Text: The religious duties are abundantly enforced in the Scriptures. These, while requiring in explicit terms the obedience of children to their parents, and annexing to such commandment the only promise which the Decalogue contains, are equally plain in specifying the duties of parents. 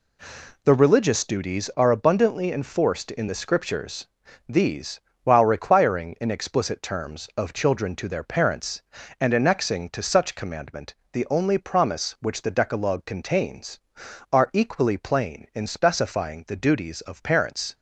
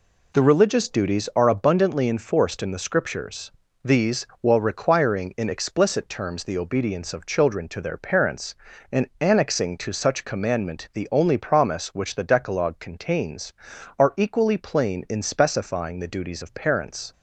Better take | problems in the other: second | skips "the obedience"; at 7.3 s // pauses between "commandment" and "the"; slight; at 10.9 s; 0.16 s long

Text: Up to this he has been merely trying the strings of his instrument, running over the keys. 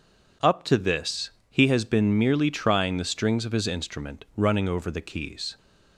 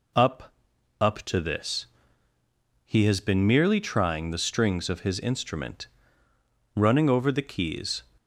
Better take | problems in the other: first | says "Up" twice; at 1.0 s // pauses between "this" and "he"; noticeable; at 1.8 s; 0.98 s long; slight in the first

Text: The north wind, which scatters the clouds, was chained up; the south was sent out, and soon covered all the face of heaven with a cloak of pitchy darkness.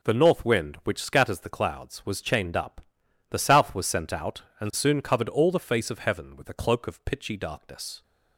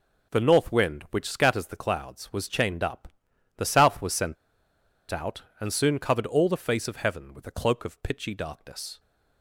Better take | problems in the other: first | pauses between "sent" and "out"; noticeable; at 4.3 s; 0.76 s long

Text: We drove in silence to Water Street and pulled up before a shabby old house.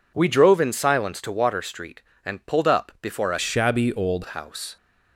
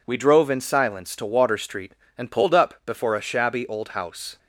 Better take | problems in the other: second | changes voice from "shabby" to "old"; from 3.3 to 4.2 s; 0.9 s long

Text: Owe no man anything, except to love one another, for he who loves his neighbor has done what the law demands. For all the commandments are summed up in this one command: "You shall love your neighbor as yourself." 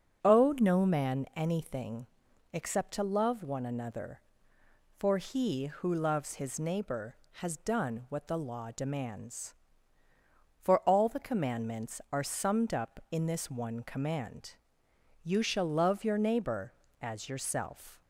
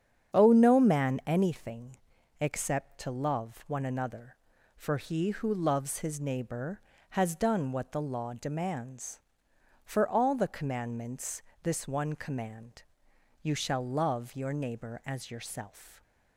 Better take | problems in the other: first | starts louder than the rest; strong; until 1.4 s; 8.5 dB // skips "are summed up in"; at 11.5 s

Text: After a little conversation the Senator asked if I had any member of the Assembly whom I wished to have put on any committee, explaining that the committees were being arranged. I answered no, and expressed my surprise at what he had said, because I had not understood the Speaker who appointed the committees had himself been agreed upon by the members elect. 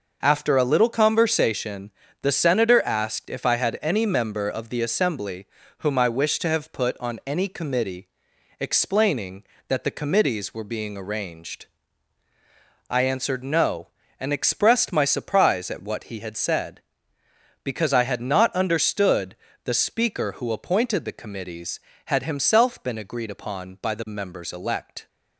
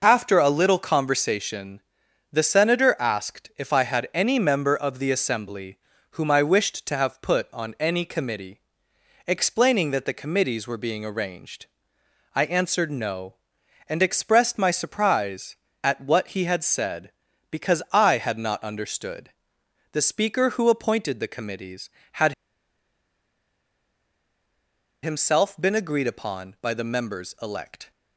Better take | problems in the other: first | pauses between "conversation" and "the"; noticeable; at 1.7 s; 0.50 s long; slight in the first // pauses between "Assembly" and "whom"; at 5.7 s; 0.42 s long; slight in the first // pauses between "understood" and "the"; noticeable; at 19.2 s; 0.64 s long; slight in the first // pauses between "had" and "himself"; strong; at 22.3 s; 2.6 s long

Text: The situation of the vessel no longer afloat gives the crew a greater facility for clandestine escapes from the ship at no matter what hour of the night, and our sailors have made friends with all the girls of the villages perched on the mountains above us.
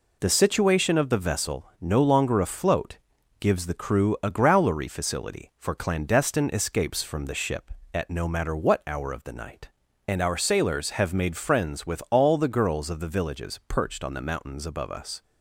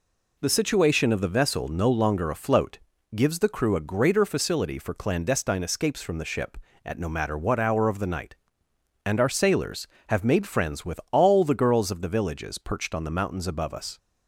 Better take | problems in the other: second | pauses between "afloat" and "gives"; at 2.9 s; 0.42 s long; also in the second // says "growlery" for "greater"; at 4.3 s

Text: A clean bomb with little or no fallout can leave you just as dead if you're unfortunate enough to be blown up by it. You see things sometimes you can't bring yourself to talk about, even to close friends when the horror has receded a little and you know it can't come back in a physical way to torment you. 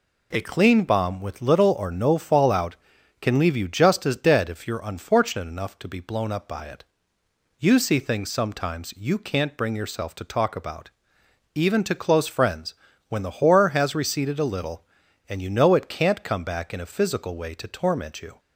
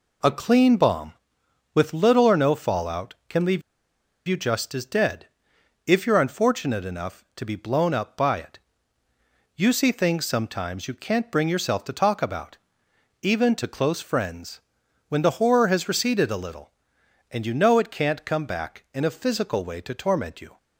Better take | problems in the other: first | pauses between "leave" and "you"; noticeable; at 3.6 s; 0.67 s long // pauses between "dead" and "if"; noticeable; at 5.2 s; 0.62 s long // pauses between "friends" and "when"; noticeable; at 14.6 s; 0.48 s long; slight in the first

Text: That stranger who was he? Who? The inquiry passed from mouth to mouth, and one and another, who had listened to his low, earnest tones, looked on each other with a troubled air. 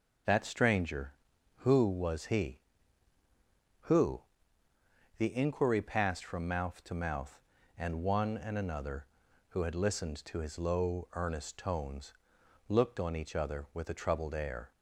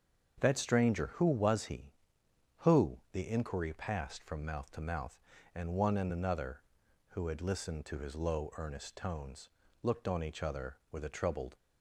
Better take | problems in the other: first | starts louder than the rest; until 1.4 s; 7 dB // stops before "air"; at 11.5 s

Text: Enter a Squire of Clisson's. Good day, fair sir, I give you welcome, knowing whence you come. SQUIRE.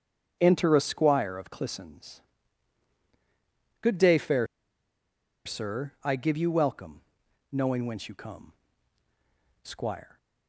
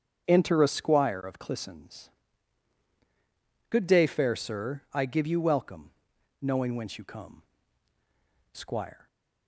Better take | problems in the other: second | starts louder than the rest; strong; until 1.4 s; 8 dB; strong in the second // pauses between "fair" and "sir"; at 4.4 s; 0.99 s long

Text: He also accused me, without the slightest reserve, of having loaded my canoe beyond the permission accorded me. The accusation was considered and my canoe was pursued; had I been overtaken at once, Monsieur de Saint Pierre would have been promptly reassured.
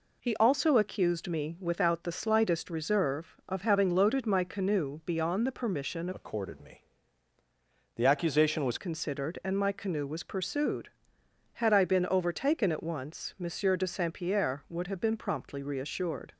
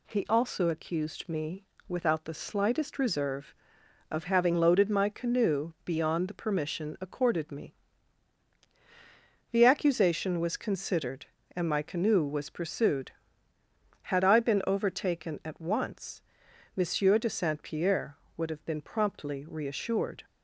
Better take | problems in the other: second | changes voice from "accorded" to "was"; from 6.1 to 8.7 s; 2.6 s long

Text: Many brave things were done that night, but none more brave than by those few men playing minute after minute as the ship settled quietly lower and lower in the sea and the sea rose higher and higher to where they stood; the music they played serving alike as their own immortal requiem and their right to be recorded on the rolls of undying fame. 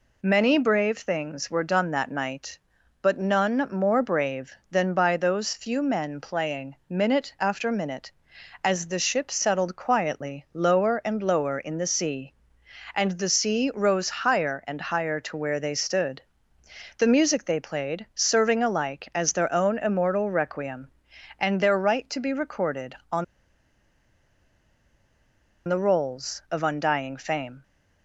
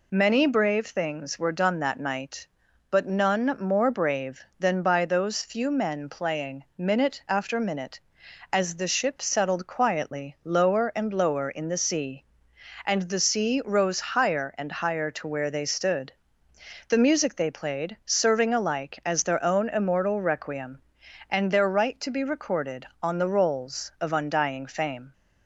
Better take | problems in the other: second | pauses between "on" and "the"; strong; at 23.2 s; 2.4 s long

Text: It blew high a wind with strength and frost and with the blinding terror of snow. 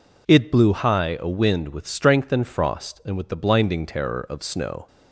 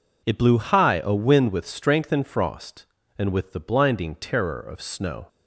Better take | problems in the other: neither | none

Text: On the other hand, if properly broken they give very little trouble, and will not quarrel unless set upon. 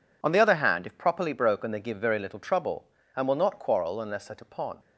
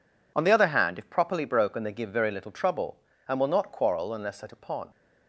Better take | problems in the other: neither | none

